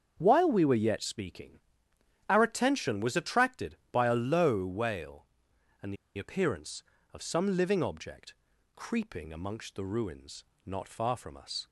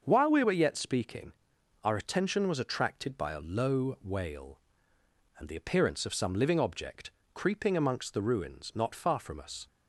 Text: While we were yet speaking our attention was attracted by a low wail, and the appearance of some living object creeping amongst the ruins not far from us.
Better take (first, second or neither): second